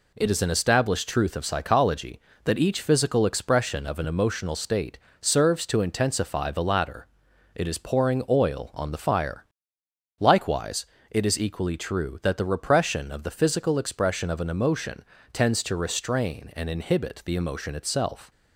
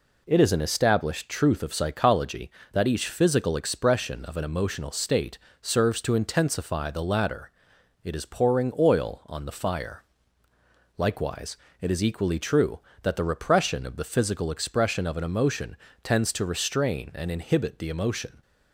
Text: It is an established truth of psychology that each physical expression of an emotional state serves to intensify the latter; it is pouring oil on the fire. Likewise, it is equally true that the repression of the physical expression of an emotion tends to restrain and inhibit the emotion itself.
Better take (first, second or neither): first